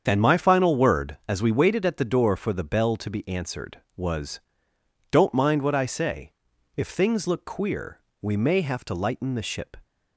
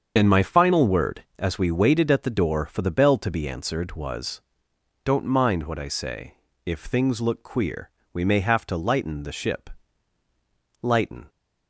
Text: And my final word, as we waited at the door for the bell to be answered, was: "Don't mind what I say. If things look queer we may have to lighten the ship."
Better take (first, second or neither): first